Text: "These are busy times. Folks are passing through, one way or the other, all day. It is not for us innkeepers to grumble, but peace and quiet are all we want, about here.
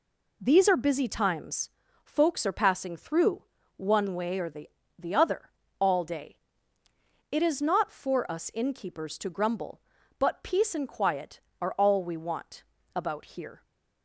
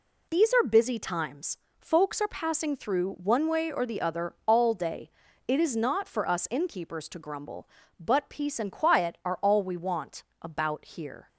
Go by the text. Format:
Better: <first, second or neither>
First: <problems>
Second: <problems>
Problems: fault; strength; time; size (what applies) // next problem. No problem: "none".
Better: second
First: says "the" twice; at 4.9 s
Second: none